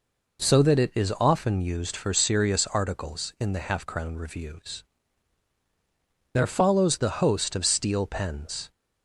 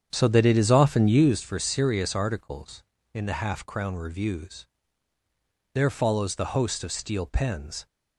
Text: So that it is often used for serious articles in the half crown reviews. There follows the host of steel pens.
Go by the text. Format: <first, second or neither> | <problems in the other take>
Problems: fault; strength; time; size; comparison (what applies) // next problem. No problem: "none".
first | starts louder than the rest; strong; until 1.3 s; 8.5 dB